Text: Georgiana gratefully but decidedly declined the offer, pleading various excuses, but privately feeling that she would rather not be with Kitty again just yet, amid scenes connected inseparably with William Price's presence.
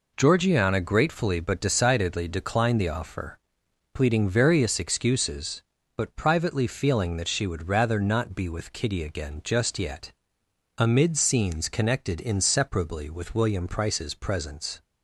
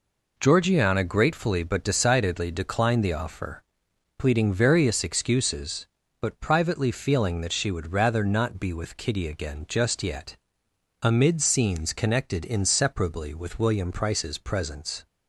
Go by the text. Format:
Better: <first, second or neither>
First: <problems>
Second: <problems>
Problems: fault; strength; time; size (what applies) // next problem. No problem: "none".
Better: neither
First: none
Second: none